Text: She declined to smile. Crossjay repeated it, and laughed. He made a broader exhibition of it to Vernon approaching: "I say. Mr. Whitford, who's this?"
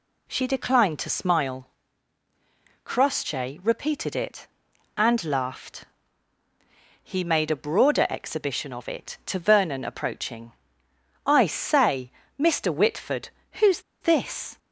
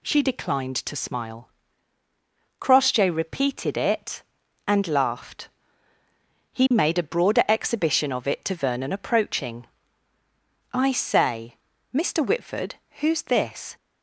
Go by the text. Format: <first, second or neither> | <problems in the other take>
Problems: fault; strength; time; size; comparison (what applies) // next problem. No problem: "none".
second | pauses between "who's" and "this"; slight; at 13.7 s; 0.20 s long